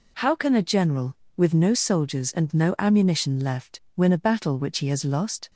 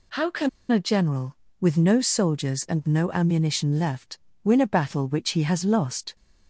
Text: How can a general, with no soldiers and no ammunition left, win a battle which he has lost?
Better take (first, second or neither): first